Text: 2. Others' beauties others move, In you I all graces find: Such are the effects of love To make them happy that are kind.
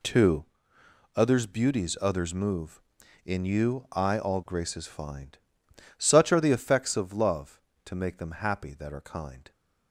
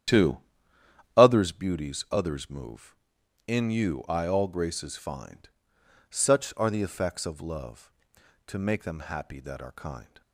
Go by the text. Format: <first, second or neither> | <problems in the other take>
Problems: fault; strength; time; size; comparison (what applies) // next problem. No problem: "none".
first | starts louder than the rest; strong; until 1.5 s; 10 dB